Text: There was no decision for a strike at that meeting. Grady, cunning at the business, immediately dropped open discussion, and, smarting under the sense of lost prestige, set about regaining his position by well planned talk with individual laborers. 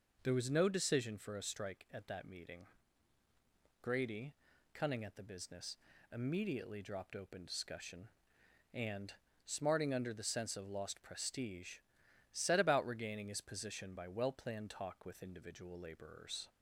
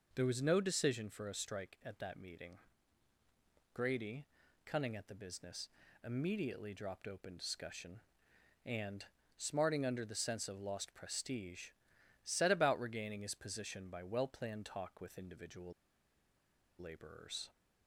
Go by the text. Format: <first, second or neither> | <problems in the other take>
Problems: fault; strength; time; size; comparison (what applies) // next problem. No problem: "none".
first | pauses between "individual" and "laborers"; at 15.7 s; 1.0 s long